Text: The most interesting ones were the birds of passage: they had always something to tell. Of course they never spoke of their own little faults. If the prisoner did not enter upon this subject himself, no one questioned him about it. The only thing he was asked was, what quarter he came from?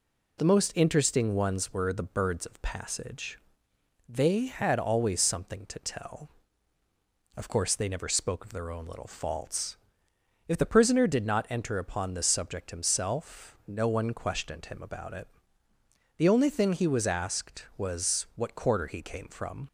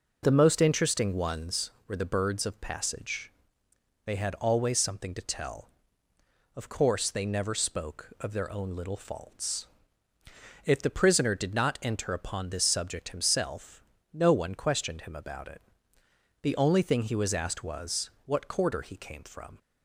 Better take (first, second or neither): neither